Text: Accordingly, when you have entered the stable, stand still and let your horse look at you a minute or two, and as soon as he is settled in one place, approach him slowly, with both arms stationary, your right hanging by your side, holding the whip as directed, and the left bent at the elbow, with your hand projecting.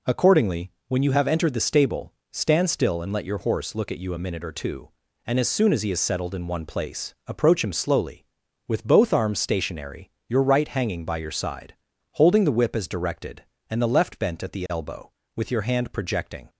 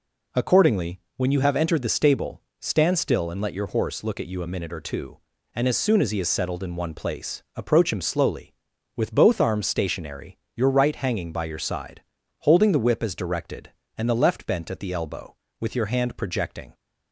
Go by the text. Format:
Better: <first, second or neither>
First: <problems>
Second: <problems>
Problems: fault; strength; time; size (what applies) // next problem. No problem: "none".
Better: neither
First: none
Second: none